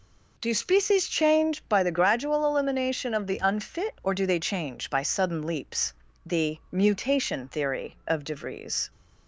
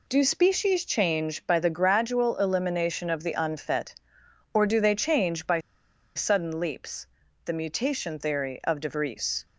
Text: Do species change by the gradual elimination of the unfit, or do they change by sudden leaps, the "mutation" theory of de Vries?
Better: first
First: none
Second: pauses between "by" and "sudden"; noticeable; at 5.5 s; 0.56 s long

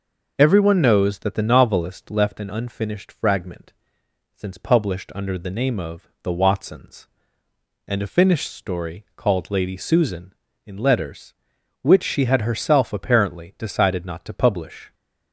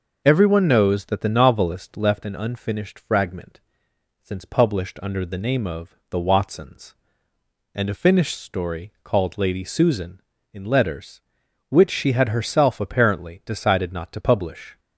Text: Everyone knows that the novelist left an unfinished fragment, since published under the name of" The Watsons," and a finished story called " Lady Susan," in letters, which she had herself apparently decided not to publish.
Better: neither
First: none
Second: none

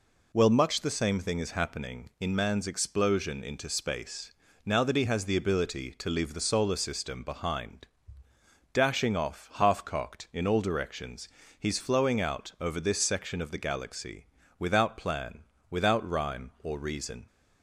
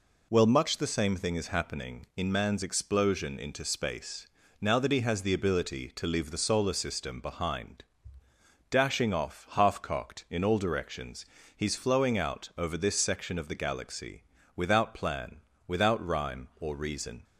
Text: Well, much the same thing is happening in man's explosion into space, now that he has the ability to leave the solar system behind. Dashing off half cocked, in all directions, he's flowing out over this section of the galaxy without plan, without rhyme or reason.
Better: neither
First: pauses between "galaxy" and "without"; slight; at 14.2 s; 0.32 s long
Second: pauses between "galaxy" and "without"; slight; at 14.2 s; 0.32 s long

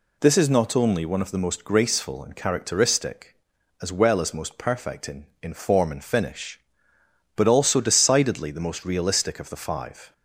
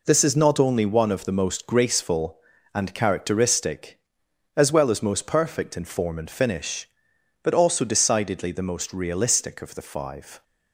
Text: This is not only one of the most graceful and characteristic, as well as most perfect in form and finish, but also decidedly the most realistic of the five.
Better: second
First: says "in" twice; at 5.4 s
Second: none

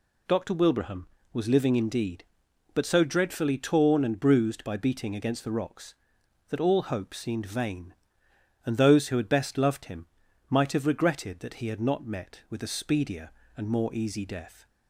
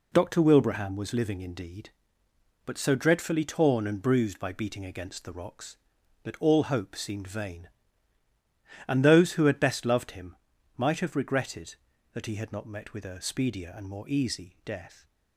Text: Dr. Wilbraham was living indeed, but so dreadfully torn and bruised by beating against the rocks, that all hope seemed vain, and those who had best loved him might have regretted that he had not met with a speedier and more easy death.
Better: neither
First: pauses between "him" and "might"; at 10.0 s; 0.44 s long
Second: pauses between "him" and "might"; at 10.3 s; 0.40 s long

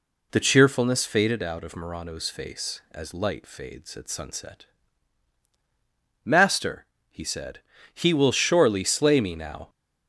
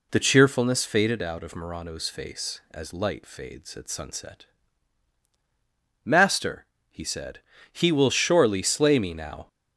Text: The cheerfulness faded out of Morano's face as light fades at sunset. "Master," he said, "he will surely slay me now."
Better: neither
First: none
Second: none

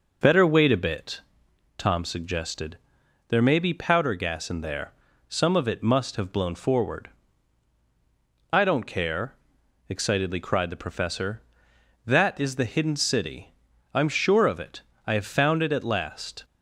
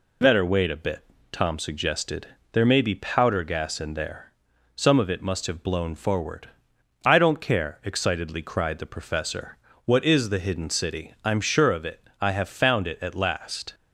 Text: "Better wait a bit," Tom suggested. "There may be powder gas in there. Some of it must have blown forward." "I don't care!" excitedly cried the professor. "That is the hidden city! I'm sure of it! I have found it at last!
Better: first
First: none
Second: says "What" for "That"; at 9.8 s

